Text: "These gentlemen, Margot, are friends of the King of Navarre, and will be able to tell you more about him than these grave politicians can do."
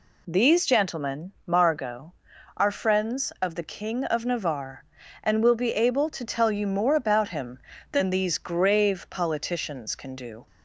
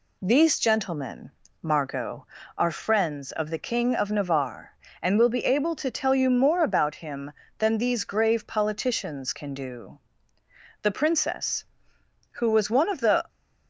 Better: first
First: none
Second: goes on to say "The princess who was one of the"; strong; from 10.8 s on; 2.4 s long

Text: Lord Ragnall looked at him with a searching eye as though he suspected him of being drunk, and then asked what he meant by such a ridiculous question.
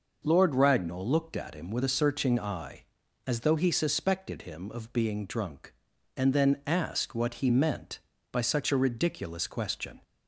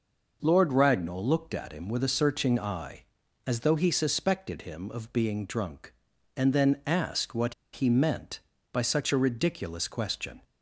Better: first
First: none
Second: pauses between "what" and "he"; slight; at 7.5 s; 0.20 s long

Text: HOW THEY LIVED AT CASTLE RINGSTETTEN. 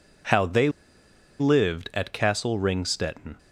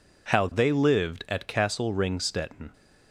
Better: second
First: pauses between "THEY" and "LIVED"; noticeable; at 0.6 s; 0.69 s long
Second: none

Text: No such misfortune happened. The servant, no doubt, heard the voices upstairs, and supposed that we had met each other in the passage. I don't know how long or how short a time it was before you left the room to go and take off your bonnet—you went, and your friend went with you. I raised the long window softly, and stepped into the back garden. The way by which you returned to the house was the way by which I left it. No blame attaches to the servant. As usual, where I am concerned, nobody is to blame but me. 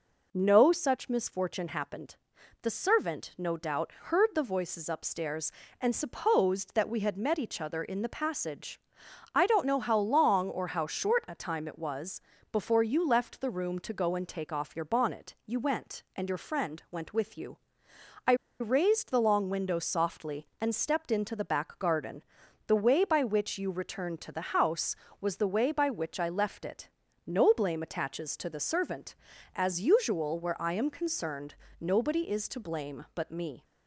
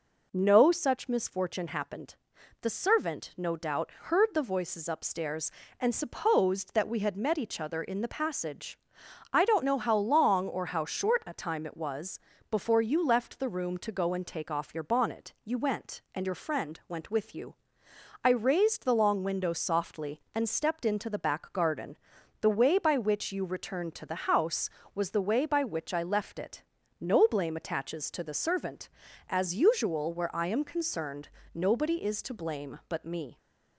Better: second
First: pauses between "was" and "before"; slight; at 12.1 s; 0.32 s long // pauses between "I" and "raised"; slight; at 18.3 s; 0.26 s long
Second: pauses between "was" and "before"; slight; at 12.1 s; 0.32 s long

